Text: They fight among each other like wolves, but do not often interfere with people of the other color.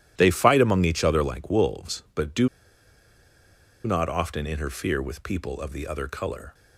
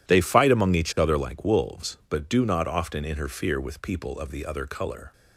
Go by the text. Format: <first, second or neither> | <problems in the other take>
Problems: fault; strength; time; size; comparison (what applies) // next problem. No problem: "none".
second | pauses between "do" and "not"; strong; at 2.4 s; 1.3 s long